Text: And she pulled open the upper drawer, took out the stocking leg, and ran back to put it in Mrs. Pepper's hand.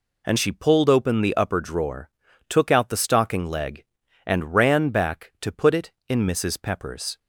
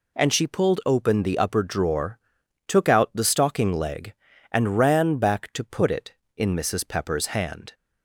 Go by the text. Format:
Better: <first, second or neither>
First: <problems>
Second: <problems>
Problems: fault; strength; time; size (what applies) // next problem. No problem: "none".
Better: second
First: stops before "hand"; at 7.1 s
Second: none